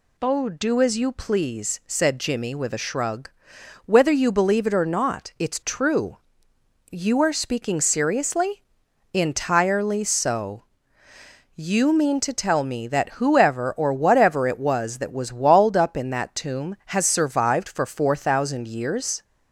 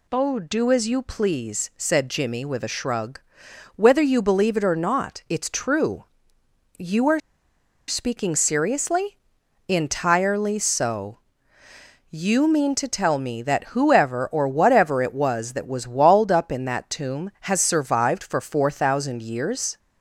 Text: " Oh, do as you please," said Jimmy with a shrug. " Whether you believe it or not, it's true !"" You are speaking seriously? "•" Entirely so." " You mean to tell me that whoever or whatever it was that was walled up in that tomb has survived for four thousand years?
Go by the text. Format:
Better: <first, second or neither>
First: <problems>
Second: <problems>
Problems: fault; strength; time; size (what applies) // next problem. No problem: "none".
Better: first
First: none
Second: pauses between "are" and "speaking"; noticeable; at 7.2 s; 0.67 s long